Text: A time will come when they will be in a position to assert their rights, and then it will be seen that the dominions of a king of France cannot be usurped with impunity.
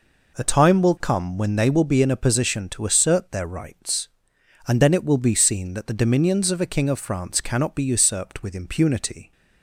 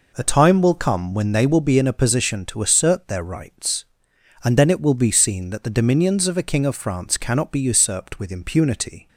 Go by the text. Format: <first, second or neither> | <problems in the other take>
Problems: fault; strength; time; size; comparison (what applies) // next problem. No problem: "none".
neither | none